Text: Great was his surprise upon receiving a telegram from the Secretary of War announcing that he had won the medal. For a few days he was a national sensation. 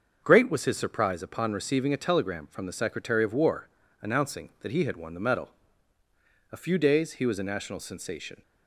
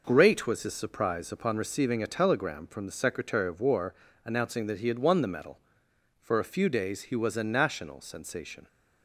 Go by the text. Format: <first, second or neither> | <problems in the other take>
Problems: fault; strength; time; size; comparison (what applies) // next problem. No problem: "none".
second | starts louder than the rest; until 1.2 s; 6.5 dB // pauses between "War" and "announcing"; slight; at 3.6 s; 0.32 s long; slight in the second // skips "For"; at 6.0 s